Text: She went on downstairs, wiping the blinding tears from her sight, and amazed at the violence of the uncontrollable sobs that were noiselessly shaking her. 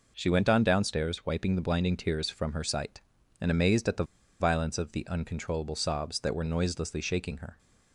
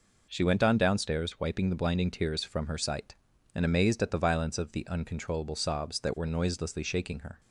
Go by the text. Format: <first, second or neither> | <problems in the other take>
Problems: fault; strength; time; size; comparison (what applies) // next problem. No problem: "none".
second | pauses between "the" and "violence"; slight; at 4.0 s; 0.34 s long